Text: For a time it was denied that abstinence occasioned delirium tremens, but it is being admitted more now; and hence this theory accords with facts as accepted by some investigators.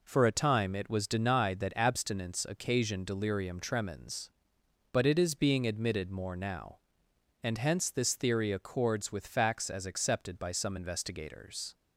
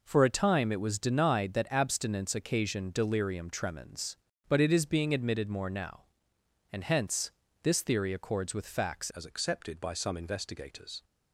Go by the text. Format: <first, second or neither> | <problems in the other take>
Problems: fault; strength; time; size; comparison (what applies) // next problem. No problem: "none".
first | pauses between "hence" and "this"; slight; at 7.3 s; 0.32 s long // changes voice at "as"; from 9.1 s on; 1.9 s long